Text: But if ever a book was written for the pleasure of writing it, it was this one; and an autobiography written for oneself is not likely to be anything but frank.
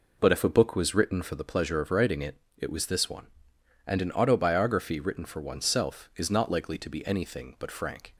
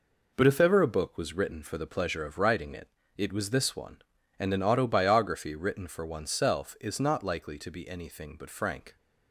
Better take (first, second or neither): second